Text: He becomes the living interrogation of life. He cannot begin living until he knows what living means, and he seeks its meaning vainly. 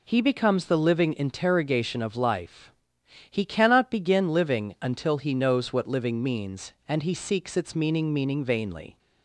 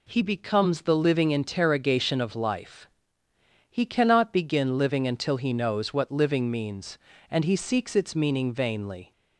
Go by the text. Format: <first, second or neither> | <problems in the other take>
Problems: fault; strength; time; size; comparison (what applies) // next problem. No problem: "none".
second | says "meaning" twice; at 8.1 s